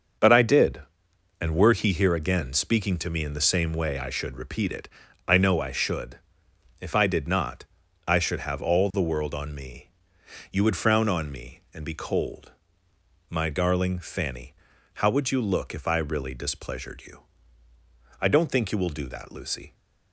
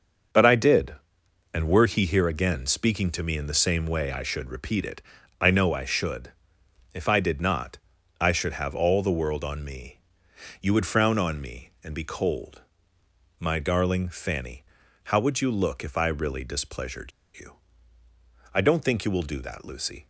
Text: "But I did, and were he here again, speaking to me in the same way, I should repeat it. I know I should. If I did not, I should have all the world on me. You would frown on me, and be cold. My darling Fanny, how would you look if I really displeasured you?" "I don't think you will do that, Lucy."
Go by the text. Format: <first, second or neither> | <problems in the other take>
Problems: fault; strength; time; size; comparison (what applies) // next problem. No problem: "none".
first | starts louder than the rest; until 1.9 s; 6.5 dB; also in the first // pauses between "displeasured" and "you"; slight; at 17.1 s; 0.26 s long